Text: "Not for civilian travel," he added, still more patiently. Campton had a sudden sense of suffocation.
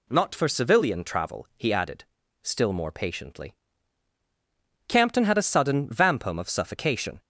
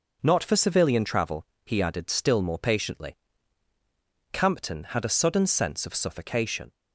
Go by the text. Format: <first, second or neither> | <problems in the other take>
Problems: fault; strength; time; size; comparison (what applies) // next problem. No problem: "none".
second | says "vampum" for "sense"; at 5.8 s